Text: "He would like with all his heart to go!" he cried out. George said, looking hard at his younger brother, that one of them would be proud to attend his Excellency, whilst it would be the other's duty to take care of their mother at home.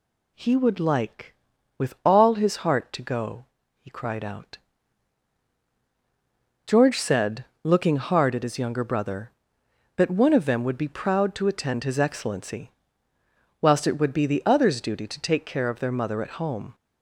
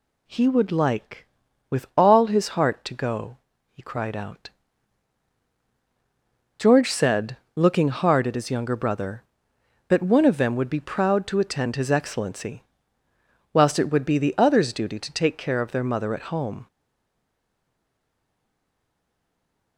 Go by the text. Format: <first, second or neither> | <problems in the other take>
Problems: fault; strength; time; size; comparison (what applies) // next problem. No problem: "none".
first | stays silent after the last word; strong; from 16.6 s on; 3.1 s long